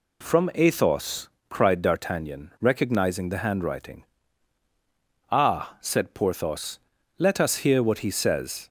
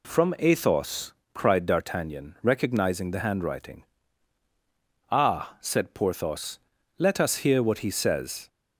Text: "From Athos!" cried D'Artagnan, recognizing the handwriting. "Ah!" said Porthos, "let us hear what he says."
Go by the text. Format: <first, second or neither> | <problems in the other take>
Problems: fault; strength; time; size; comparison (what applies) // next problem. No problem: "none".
neither | none